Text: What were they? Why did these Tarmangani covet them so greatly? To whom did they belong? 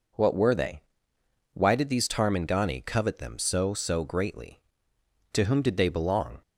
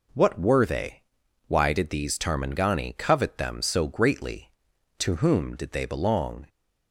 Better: second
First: says "so" twice; at 3.7 s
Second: none

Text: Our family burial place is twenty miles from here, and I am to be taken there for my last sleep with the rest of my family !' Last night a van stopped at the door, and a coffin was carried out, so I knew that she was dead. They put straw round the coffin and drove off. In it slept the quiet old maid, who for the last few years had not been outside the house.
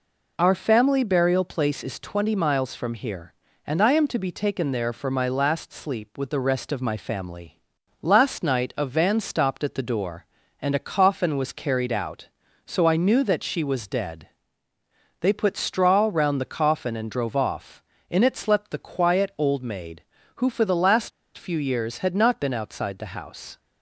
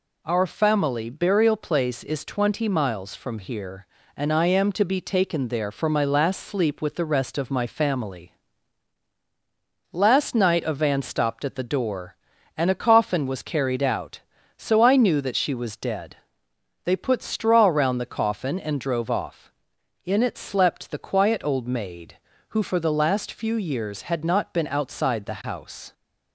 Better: second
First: pauses between "last" and "few"; slight; at 21.1 s; 0.26 s long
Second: none

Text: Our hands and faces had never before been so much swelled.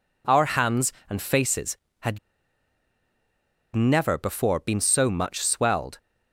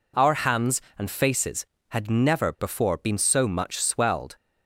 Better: second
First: pauses between "had" and "never"; strong; at 2.1 s; 1.5 s long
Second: none

